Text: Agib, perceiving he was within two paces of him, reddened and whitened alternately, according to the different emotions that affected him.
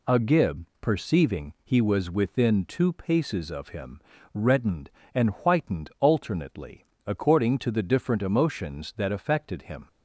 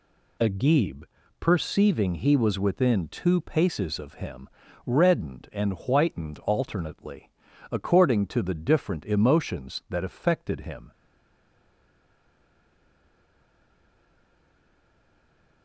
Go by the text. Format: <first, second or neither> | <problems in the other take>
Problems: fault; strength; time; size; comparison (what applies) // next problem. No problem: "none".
first | stays silent after the last word; strong; from 10.9 s on; 4.7 s long